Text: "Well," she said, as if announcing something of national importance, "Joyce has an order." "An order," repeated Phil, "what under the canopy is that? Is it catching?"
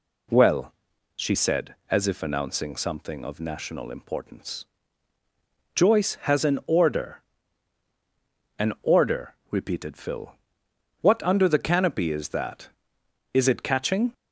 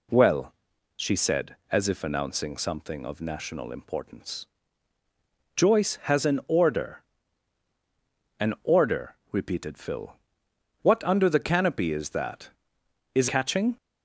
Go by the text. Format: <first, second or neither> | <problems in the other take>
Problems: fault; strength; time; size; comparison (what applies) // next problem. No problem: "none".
first | skips "it"; at 13.2 s